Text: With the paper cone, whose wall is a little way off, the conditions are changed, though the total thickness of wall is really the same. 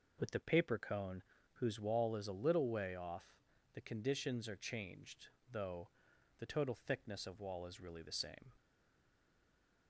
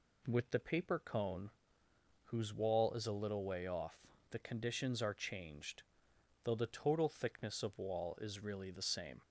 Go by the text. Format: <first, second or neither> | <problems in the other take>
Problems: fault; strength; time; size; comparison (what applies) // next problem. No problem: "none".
second | pauses between "though" and "the"; noticeable; at 5.8 s; 0.52 s long // stays silent after the last word; noticeable; from 8.5 s on; 1.3 s long